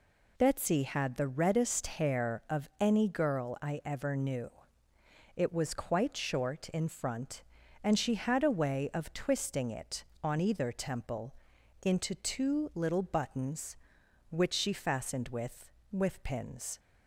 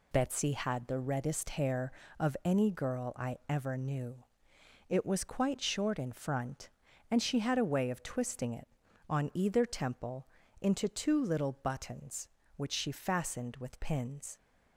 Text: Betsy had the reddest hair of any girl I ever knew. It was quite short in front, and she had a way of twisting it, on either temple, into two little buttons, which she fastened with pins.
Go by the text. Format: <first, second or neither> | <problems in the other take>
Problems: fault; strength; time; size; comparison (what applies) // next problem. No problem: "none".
second | says "with" twice; at 15.9 s